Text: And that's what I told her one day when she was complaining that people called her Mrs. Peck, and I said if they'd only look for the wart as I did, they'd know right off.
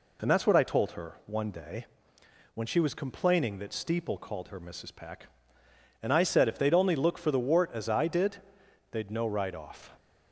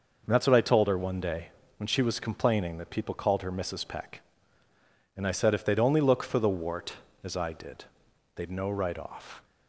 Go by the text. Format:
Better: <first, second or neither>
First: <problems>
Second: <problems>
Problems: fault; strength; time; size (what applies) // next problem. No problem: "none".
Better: second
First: pauses between "day" and "when"; noticeable; at 1.8 s; 0.66 s long // says "steeple" for "people"; at 3.7 s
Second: pauses between "day" and "when"; slight; at 1.4 s; 0.28 s long